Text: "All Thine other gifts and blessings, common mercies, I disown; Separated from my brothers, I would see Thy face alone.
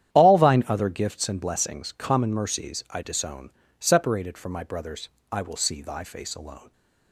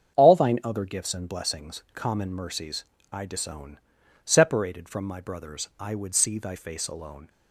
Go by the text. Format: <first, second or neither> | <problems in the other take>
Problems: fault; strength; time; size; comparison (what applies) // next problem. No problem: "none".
second | starts louder than the rest; strong; until 1.1 s; 10.5 dB; strong in the second // says "will" for "would"; at 5.4 s